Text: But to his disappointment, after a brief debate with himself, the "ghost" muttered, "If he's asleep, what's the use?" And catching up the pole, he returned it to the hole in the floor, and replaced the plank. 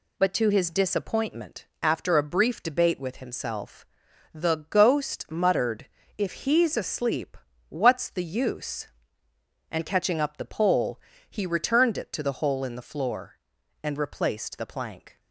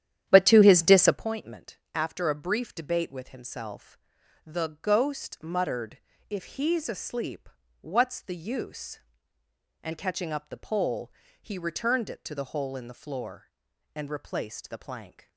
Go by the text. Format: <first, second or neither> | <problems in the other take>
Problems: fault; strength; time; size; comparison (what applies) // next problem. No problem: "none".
first | starts louder than the rest; strong; until 1.2 s; 10.5 dB